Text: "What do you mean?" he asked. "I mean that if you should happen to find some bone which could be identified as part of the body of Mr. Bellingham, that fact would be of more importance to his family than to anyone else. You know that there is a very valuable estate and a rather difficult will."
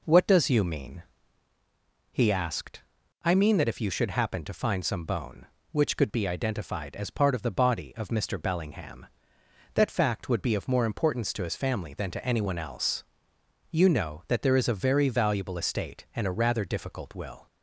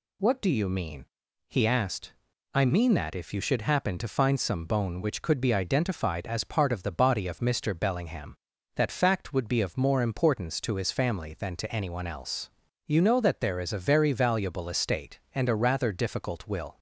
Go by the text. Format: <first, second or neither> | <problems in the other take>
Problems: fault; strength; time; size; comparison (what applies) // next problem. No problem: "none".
second | says "does" for "do"; at 0.2 s